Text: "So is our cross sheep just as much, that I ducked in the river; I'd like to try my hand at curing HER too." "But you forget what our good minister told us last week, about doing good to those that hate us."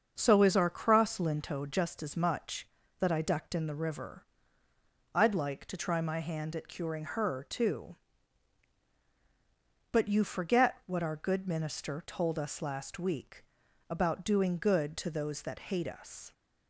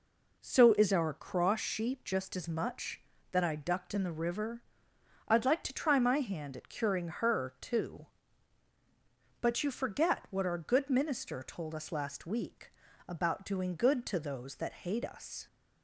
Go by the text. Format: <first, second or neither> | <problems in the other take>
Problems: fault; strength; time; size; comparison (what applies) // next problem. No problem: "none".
second | starts louder than the rest; until 1.1 s; 6.5 dB // says "linto" for "sheep"; at 1.1 s